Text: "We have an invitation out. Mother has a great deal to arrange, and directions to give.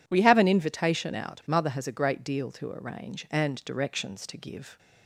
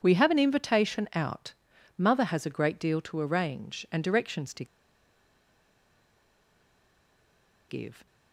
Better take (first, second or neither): first